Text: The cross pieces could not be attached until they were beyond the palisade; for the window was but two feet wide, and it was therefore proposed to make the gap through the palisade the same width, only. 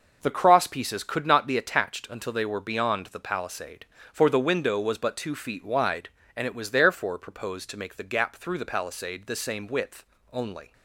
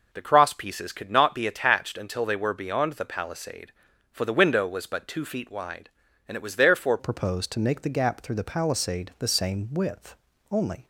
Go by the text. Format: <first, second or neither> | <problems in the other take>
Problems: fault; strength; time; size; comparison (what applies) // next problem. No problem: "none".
first | changes voice at "proposed"; from 6.9 s on; 3.9 s long